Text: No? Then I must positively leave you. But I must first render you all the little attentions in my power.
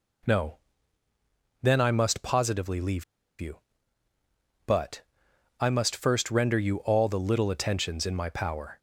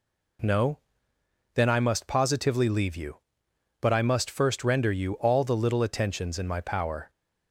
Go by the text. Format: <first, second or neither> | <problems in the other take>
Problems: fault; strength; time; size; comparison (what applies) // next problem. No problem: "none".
second | pauses between "leave" and "you"; at 3.0 s; 0.36 s long // pauses between "But" and "I"; noticeable; at 5.0 s; 0.58 s long